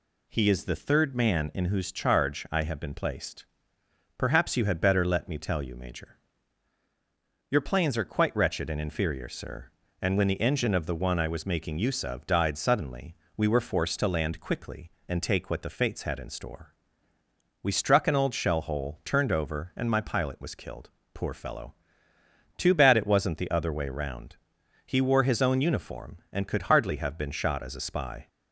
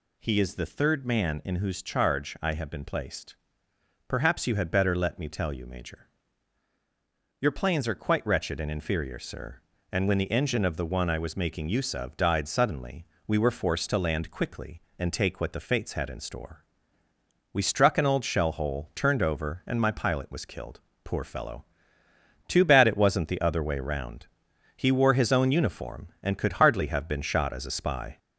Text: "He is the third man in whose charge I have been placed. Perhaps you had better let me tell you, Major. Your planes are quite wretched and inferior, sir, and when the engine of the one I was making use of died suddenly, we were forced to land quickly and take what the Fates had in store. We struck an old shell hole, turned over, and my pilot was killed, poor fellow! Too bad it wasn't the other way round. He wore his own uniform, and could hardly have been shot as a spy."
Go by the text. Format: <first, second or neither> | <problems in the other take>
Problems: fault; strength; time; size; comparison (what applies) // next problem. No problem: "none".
first | gets louder; slight; throughout; 3 dB